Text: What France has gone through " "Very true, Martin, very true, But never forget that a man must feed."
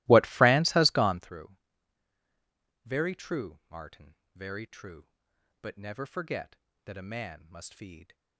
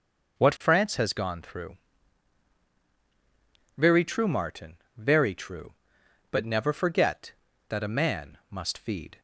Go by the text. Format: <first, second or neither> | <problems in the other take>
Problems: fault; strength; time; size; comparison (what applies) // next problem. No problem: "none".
second | starts louder than the rest; strong; until 1.3 s; 19 dB